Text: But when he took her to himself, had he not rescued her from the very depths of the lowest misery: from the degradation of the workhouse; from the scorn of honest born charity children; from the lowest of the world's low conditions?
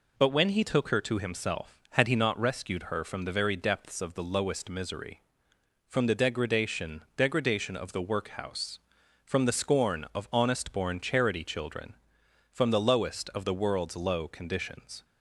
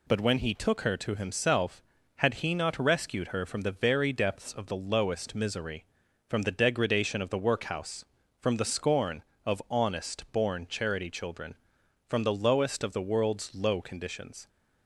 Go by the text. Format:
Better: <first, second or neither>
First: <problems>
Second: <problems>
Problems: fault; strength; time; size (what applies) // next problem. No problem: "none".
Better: second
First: says "degradation" twice; at 7.1 s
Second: none